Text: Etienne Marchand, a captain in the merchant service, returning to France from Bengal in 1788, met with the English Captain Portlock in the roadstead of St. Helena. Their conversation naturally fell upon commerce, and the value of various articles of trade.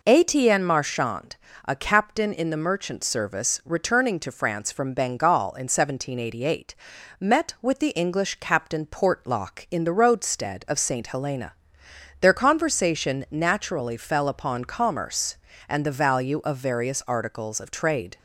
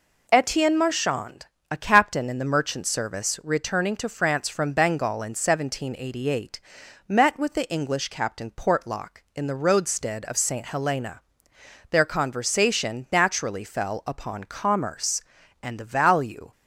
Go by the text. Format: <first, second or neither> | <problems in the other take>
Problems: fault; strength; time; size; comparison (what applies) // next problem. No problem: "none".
first | stops before "of various articles of trade"; at 16.5 s